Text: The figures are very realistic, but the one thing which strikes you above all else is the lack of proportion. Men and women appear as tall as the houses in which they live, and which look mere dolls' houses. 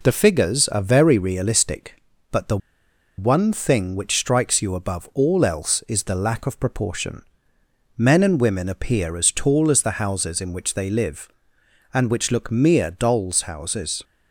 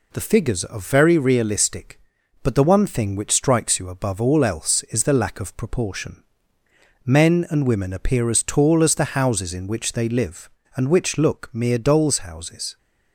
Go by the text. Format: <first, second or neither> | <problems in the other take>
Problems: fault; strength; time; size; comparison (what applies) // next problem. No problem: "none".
second | pauses between "the" and "one"; noticeable; at 2.5 s; 0.60 s long